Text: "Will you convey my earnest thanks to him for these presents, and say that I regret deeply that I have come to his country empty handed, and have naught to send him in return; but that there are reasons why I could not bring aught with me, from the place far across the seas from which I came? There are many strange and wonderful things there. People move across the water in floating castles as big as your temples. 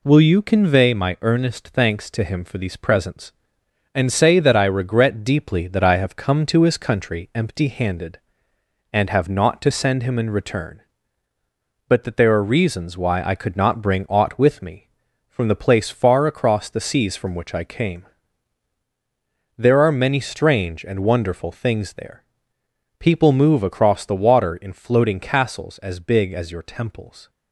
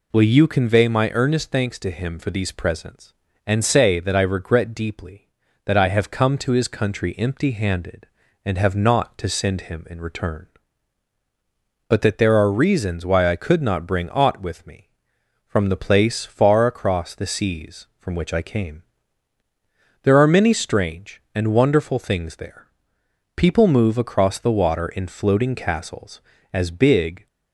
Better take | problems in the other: first | stops before "as your temples"; at 27.2 s

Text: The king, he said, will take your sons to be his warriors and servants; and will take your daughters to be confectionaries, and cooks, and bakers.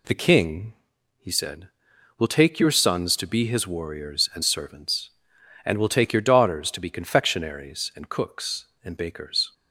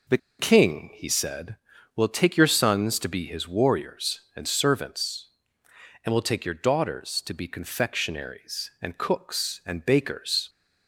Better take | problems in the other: first | pauses between "The" and "king"; slight; at 0.1 s; 0.21 s long

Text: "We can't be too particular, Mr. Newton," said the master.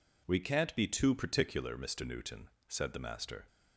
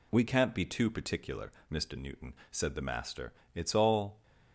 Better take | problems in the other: first | goes on to say "It's all"; noticeable; from 3.5 s on; 0.68 s long

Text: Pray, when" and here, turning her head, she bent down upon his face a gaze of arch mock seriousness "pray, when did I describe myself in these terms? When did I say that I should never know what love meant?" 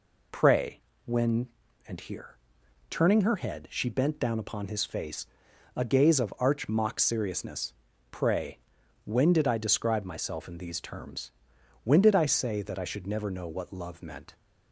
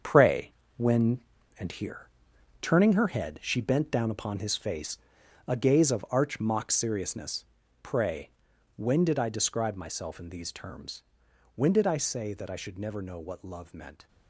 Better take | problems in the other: first | gets quieter; strong; throughout; 10 dB // pauses between "face" and "a"; noticeable; at 4.9 s; 0.50 s long; noticeable in the first // pauses between "seriousness" and "pray"; at 7.4 s; 0.38 s long; also in the first

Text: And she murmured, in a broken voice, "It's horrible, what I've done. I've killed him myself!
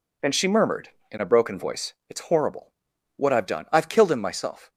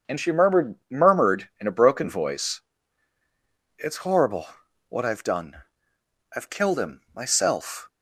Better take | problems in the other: first | starts louder than the rest; until 1.2 s; 6.5 dB // says "murmured" twice; at 0.8 s

